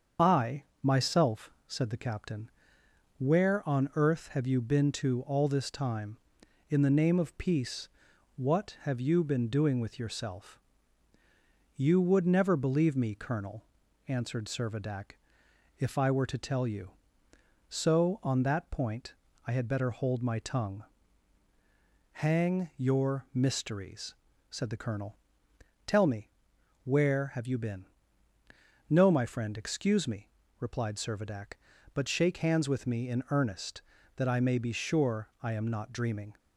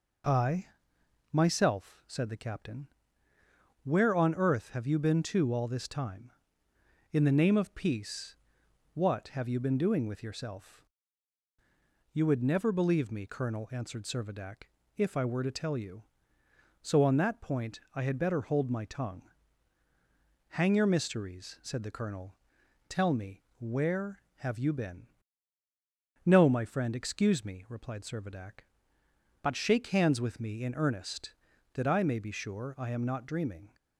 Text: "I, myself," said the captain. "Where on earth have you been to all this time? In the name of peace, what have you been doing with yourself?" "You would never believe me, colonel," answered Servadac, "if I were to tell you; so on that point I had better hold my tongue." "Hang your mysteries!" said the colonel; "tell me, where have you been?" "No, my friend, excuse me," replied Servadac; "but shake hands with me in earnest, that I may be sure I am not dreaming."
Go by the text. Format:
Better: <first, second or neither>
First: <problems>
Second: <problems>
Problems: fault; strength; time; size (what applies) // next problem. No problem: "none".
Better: second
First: loses the start of "I"; at 0.1 s; 25 ms // starts louder than the rest; strong; until 1.3 s; 7 dB // pauses between "point" and "I"; slight; at 19.1 s; 0.32 s long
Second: none